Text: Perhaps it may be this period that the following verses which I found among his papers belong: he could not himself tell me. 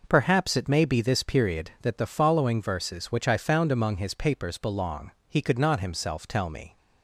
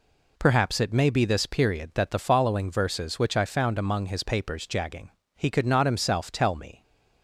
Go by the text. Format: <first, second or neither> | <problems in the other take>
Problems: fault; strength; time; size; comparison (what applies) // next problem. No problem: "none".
first | says "jagging" for "belong"; at 4.6 s